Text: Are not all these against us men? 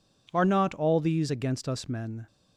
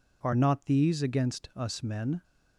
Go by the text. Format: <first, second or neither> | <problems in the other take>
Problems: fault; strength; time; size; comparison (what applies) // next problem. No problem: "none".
first | skips "all"; at 0.6 s